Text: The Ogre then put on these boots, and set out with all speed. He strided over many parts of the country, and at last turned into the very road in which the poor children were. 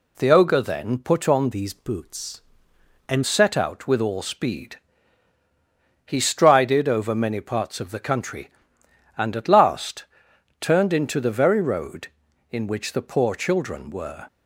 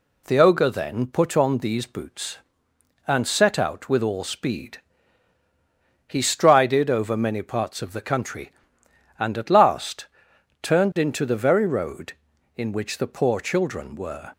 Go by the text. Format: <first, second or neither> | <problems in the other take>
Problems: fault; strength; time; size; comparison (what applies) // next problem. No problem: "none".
second | changes voice from "these" to "and"; from 1.5 to 3.2 s; 1.7 s long // pauses between "last" and "turned"; noticeable; at 10.0 s; 0.56 s long; noticeable in the second